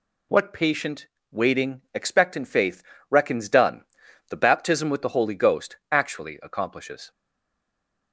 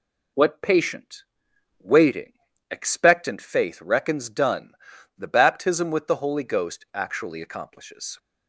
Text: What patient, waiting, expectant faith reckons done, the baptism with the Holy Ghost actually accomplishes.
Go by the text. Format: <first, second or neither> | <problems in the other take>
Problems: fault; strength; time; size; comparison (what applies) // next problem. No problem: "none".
second | pauses between "faith" and "reckons"; slight; at 2.8 s; 0.26 s long // pauses between "Ghost" and "actually"; slight; at 5.7 s; 0.16 s long // stays silent after the last word; from 7.1 s on; 1.0 s long